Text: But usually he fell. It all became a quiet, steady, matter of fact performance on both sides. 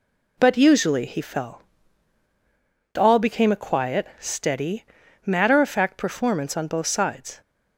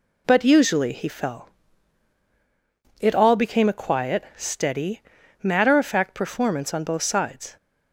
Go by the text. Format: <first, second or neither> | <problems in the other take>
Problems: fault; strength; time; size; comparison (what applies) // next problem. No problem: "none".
second | skips "It"; at 2.2 s